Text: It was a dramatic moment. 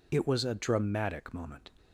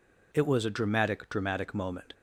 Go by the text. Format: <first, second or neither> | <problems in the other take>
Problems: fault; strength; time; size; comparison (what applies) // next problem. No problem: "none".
first | says "dramatic" twice; at 1.3 s